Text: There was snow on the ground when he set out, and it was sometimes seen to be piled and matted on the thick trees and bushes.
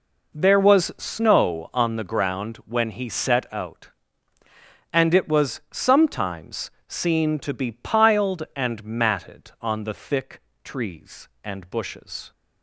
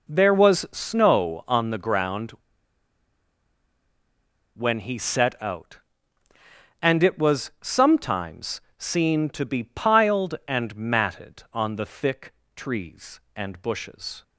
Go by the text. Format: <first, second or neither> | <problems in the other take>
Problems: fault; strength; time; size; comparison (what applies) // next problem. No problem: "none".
first | pauses between "ground" and "when"; strong; at 2.2 s; 2.2 s long // pauses between "sometimes" and "seen"; slight; at 8.6 s; 0.18 s long; slight in the first // pauses between "thick" and "trees"; slight; at 12.3 s; 0.24 s long; slight in the first